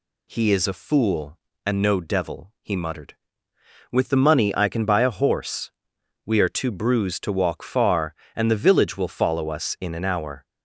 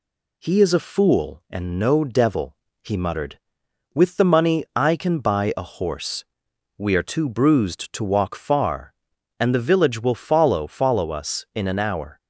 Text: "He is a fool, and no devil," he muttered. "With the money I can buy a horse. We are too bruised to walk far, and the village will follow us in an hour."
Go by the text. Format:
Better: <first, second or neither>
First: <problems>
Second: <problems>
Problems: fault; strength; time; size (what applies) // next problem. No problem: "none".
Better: first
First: none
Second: says "follow" twice; at 10.6 s